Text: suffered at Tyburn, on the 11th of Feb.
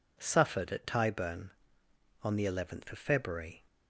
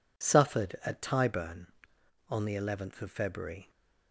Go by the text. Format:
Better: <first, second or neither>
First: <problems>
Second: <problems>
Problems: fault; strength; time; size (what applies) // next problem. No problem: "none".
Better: neither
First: none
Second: none